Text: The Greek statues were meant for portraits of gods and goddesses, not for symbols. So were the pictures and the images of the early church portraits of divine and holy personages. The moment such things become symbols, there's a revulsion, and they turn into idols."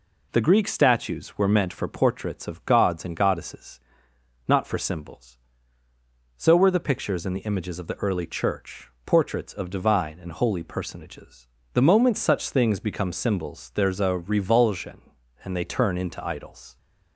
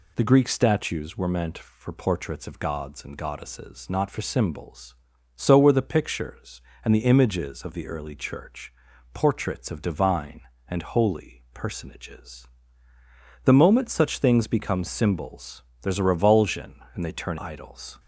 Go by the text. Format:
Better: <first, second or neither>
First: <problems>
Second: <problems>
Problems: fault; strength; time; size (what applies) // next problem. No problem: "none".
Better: first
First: pauses between "church" and "portraits"; slight; at 8.8 s; 0.16 s long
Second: pauses between "church" and "portraits"; at 8.7 s; 0.40 s long // skips "into"; at 17.3 s